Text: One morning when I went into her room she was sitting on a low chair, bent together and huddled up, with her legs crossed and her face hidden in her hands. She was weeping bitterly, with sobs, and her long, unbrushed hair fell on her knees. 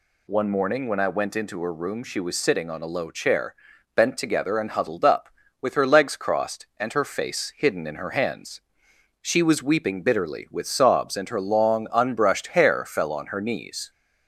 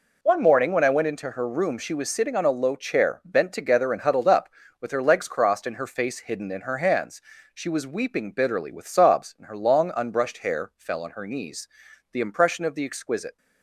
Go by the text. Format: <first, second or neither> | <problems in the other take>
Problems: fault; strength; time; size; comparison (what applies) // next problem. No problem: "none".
first | goes on to say "The impression of the exquisite"; noticeable; from 12.1 s on; 1.2 s long